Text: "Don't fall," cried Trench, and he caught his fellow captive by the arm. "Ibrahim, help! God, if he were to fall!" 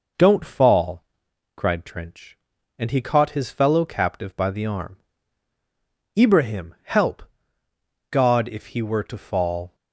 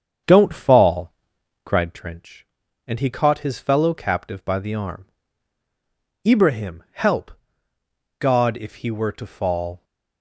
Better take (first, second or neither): first